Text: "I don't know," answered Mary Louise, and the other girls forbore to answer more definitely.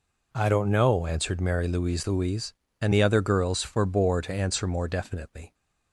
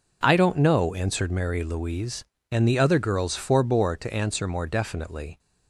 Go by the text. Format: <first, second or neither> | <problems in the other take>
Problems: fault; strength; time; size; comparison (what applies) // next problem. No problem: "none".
second | says "Louise" twice; at 2.0 s